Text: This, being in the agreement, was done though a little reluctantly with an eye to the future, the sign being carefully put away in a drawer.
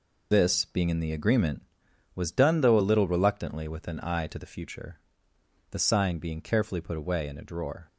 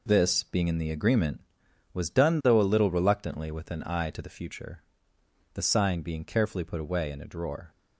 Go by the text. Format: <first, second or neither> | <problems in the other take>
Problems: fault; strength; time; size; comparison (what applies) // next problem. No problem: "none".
second | loses the start of "This"; at 0.3 s; 35 ms